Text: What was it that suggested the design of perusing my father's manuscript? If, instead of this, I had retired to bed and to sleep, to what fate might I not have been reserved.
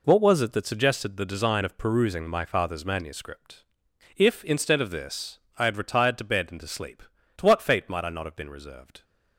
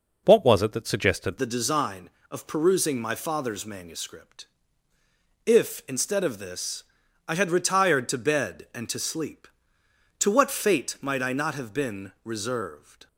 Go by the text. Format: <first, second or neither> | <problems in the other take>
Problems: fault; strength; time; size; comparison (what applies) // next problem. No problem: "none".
first | changes voice at "the"; from 1.3 s on; 11.7 s long